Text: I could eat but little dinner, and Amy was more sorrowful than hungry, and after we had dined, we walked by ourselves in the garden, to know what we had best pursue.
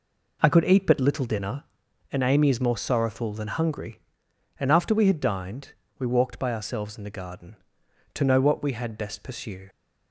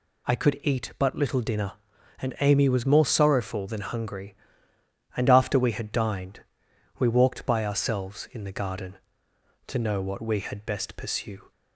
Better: second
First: says "is" for "was"; at 2.4 s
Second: none

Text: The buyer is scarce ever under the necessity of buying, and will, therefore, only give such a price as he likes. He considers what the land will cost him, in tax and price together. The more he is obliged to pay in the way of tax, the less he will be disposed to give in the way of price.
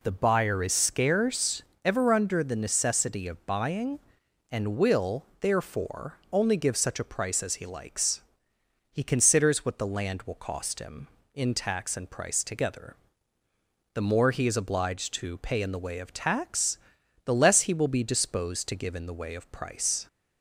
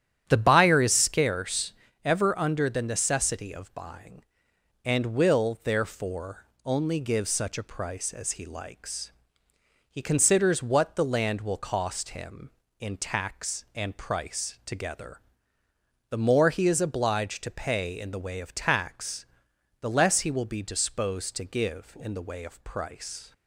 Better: first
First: pauses between "scarce" and "ever"; slight; at 1.6 s; 0.24 s long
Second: starts louder than the rest; strong; until 1.3 s; 11 dB // pauses between "scarce" and "ever"; slight; at 1.7 s; 0.32 s long

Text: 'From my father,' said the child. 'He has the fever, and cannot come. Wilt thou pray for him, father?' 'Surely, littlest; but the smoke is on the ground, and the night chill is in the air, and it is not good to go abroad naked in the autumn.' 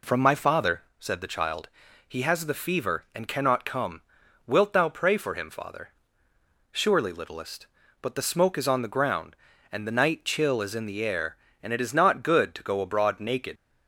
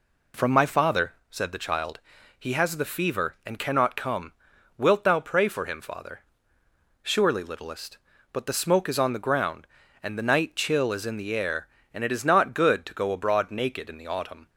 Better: second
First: stops before "in the autumn"; at 13.5 s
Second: none

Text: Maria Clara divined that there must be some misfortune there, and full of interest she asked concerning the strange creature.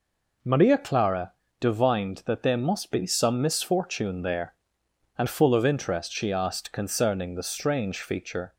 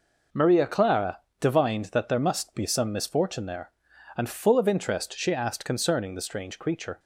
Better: second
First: pauses between "Clara" and "divined"; slight; at 1.3 s; 0.26 s long // says "feature" for "creature"; at 7.9 s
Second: pauses between "Clara" and "divined"; slight; at 1.1 s; 0.22 s long

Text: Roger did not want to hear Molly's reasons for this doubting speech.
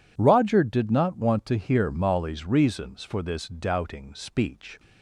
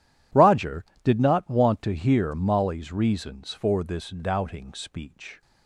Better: neither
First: none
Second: none

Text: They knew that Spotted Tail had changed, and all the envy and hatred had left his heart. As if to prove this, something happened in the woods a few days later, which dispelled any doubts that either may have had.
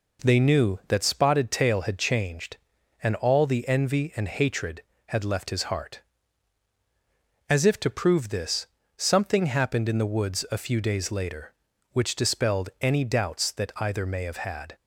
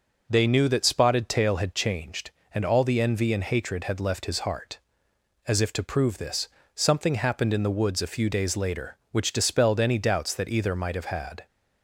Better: first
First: none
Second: says "might" for "may"; at 10.7 s

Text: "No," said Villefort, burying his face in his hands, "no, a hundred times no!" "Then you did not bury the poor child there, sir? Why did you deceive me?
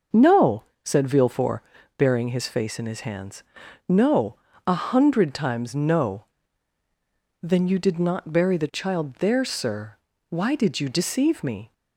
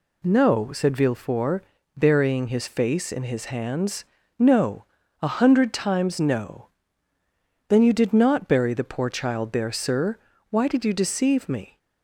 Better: second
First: starts louder than the rest; noticeable; until 1.3 s; 6 dB // skips "poor"; at 8.7 s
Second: none

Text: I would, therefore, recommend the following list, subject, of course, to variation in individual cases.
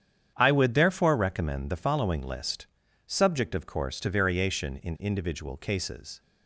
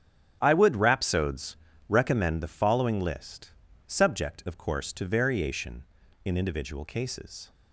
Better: first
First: starts louder than the rest; strong; until 1.3 s; 8.5 dB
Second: starts louder than the rest; strong; until 1.4 s; 10 dB // says "rhapsodes" for "therefore"; at 0.7 s

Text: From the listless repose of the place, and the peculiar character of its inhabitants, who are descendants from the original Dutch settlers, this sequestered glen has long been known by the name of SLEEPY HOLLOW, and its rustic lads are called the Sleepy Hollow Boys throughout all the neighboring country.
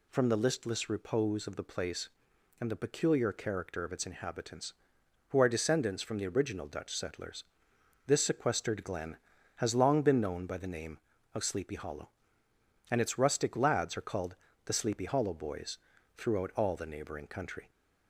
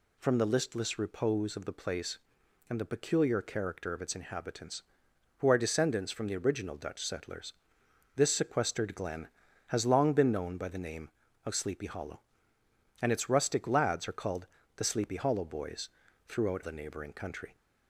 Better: first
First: pauses between "called" and "the"; slight; at 14.3 s; 0.30 s long // pauses between "Boys" and "throughout"; at 15.7 s; 0.38 s long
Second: pauses between "called" and "the"; slight; at 14.4 s; 0.30 s long // pauses between "Boys" and "throughout"; at 15.8 s; 0.38 s long // skips "all"; at 16.6 s

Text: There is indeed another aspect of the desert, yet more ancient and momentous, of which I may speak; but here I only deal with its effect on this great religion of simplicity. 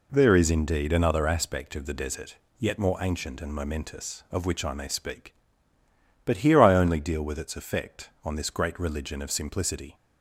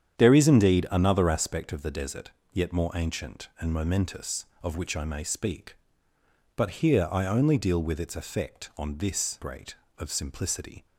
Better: first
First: none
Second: starts louder than the rest; strong; until 1.2 s; 9 dB // skips "religion"; at 9.8 s

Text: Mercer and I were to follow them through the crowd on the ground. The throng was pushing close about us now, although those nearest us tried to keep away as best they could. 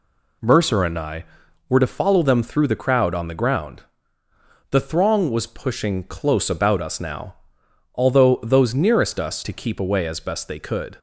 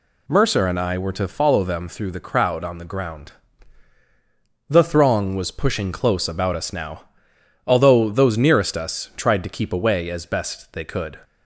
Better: second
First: skips "tried"; at 9.4 s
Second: none

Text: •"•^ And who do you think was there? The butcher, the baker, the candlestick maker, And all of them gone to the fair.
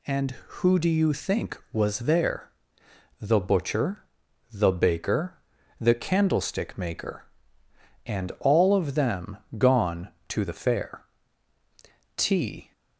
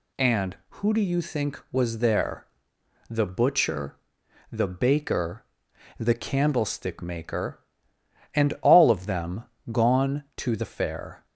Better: second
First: pauses between "them" and "gone"; slight; at 9.3 s; 0.20 s long // goes on to say "T"; from 12.1 s on; 0.56 s long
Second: pauses between "them" and "gone"; slight; at 9.4 s; 0.26 s long

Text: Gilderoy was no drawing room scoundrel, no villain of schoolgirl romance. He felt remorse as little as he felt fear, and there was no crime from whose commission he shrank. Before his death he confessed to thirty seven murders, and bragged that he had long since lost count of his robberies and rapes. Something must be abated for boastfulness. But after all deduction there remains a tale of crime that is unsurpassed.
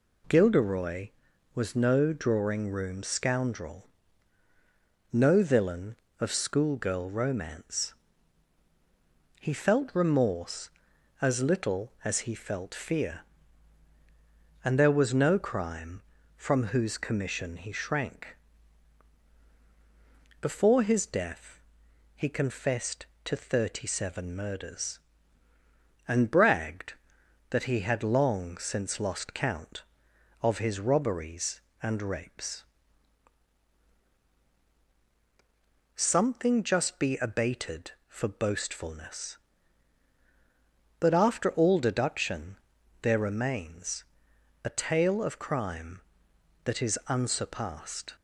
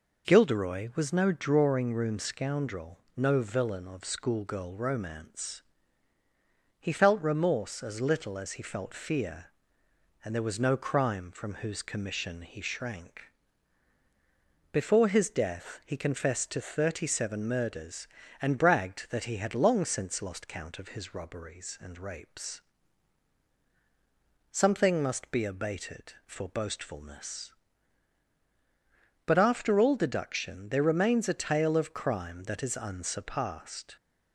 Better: second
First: pauses between "death" and "he"; noticeable; at 21.5 s; 0.56 s long // says "just" for "must"; at 36.6 s // pauses between "deduction" and "there"; at 42.5 s; 0.44 s long // pauses between "remains" and "a"; noticeable; at 44.0 s; 0.60 s long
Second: none

